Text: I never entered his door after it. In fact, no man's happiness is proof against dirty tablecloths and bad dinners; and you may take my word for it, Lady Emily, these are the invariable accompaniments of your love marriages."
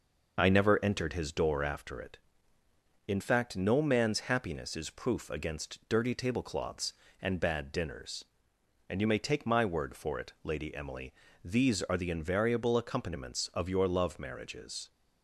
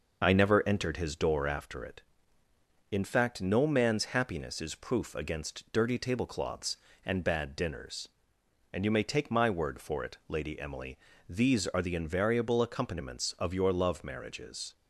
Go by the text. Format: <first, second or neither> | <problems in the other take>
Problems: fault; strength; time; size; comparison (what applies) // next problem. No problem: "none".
neither | none